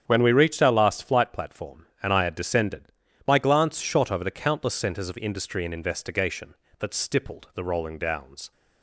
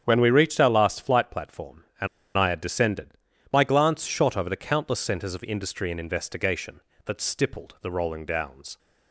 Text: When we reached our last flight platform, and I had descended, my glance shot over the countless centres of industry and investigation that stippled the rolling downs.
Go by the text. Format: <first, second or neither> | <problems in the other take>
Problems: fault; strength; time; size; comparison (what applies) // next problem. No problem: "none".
first | starts louder than the rest; strong; until 1.0 s; 8.5 dB; strong in the first // pauses between "and" and "I"; slight; at 2.0 s; 0.30 s long